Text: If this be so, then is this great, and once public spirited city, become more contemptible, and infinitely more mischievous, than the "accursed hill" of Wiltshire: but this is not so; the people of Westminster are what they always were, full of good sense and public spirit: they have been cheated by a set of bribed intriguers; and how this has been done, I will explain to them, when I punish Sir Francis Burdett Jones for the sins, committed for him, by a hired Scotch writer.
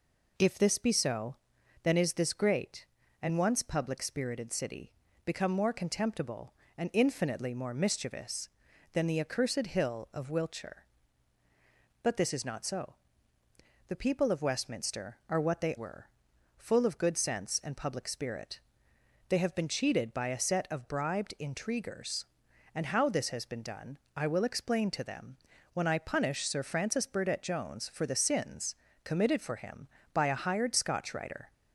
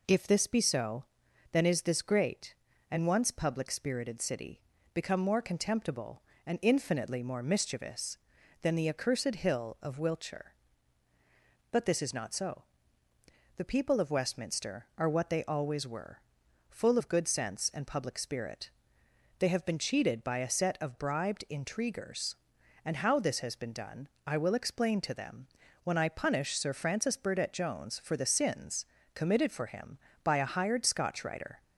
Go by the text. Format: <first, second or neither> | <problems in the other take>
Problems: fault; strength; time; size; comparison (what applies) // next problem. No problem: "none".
second | skips "always"; at 15.7 s